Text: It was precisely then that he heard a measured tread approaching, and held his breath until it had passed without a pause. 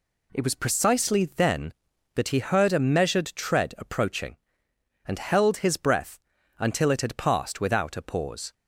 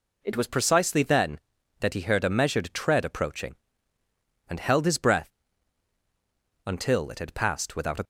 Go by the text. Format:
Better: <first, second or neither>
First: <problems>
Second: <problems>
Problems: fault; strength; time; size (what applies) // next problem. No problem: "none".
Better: first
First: pauses between "breath" and "until"; at 6.1 s; 0.40 s long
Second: pauses between "breath" and "until"; strong; at 5.2 s; 1.3 s long // stops before "pause"; at 8.0 s